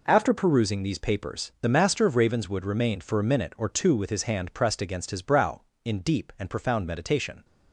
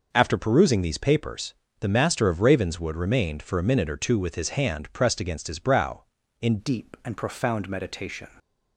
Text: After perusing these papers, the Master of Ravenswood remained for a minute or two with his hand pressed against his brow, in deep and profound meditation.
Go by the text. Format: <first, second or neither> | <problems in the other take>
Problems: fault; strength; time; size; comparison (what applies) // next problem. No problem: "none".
first | changes voice at "deep"; from 6.5 s on; 1.7 s long